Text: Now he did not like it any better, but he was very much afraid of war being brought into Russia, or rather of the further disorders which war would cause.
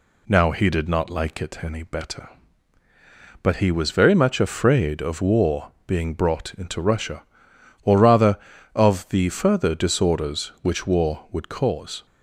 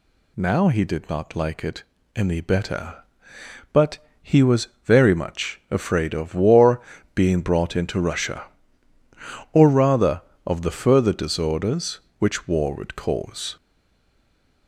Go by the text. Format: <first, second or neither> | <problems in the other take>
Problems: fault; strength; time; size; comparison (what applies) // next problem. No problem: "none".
first | pauses between "it" and "any"; slight; at 1.8 s; 0.32 s long // pauses between "but" and "he"; slight; at 3.9 s; 0.22 s long // pauses between "was" and "very"; slight; at 4.6 s; 0.16 s long // pauses between "war" and "being"; slight; at 6.7 s; 0.34 s long; slight in the first // stays silent after the last word; from 13.5 s on; 1.1 s long